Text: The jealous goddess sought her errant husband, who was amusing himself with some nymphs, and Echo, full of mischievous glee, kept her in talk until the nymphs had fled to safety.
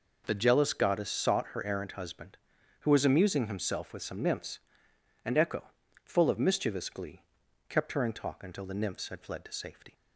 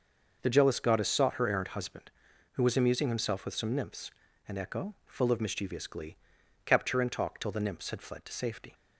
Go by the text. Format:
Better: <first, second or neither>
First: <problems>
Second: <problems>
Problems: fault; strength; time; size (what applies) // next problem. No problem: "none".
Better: first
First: none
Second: says "till" for "until"; at 7.3 s